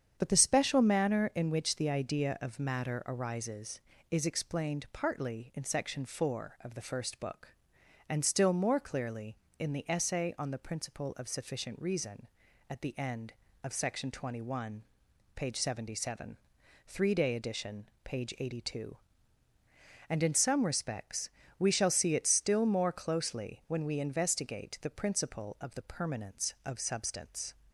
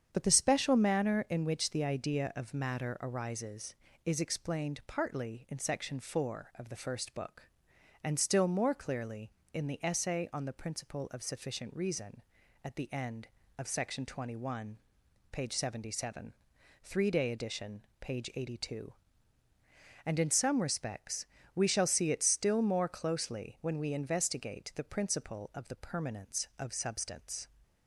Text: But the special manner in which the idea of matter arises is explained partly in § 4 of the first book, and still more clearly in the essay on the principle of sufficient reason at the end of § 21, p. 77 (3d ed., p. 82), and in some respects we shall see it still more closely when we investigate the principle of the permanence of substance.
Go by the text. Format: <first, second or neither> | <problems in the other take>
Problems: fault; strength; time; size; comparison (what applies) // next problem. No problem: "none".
neither | starts louder than the rest; strong; the same in both // pauses between "respects" and "we"; slight; the same in both